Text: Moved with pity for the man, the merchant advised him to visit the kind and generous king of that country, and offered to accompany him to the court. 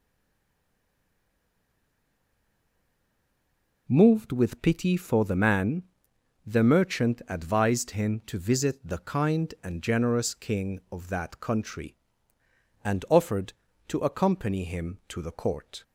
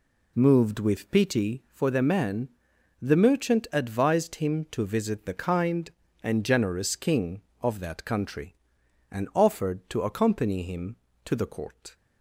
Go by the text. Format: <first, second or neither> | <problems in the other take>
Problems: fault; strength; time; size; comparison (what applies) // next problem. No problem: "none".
second | stays silent before the first word; strong; until 3.8 s; 3.8 s long